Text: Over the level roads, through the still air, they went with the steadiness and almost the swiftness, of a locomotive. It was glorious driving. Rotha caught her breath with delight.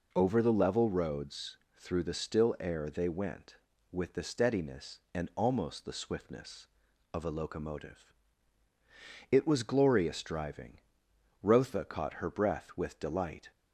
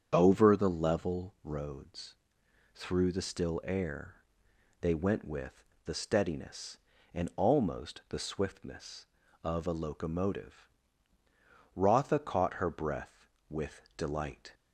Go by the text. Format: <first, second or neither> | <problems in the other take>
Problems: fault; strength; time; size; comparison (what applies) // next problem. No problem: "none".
first | starts louder than the rest; strong; until 1.1 s; 8 dB // pauses between "with" and "the"; slight; at 5.6 s; 0.22 s long // skips "It was glorious driving"; at 11.2 s // pauses between "with" and "delight"; slight; at 13.8 s; 0.16 s long